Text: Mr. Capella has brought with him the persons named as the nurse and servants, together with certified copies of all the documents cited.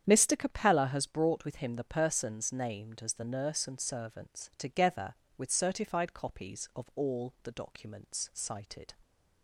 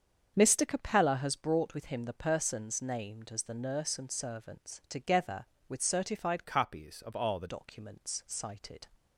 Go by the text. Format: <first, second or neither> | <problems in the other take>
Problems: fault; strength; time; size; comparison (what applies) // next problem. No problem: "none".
first | starts louder than the rest; strong; until 1.3 s; 7.5 dB; strong in the first // changes voice from "copies" to "the"; from 6.4 to 7.4 s; 1.0 s long